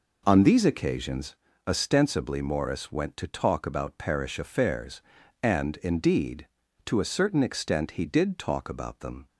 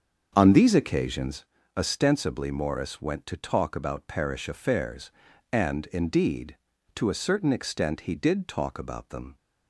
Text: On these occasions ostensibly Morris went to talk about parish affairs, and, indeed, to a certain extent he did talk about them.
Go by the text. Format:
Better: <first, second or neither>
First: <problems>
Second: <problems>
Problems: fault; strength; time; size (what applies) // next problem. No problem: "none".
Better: first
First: pauses between "occasions" and "ostensibly"; slight; at 1.3 s; 0.32 s long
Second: starts louder than the rest; until 1.4 s; 7 dB // pauses between "occasions" and "ostensibly"; slight; at 1.4 s; 0.32 s long